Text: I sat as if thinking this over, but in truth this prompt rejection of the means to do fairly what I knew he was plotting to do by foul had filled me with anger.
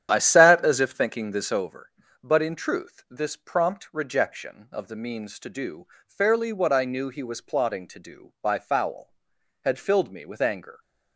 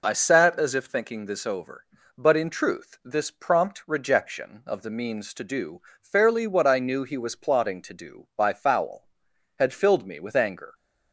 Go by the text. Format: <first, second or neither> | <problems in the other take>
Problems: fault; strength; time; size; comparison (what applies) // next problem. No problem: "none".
second | starts louder than the rest; strong; until 1.7 s; 10 dB // pauses between "do" and "fairly"; slight; at 5.8 s; 0.18 s long; slight in the second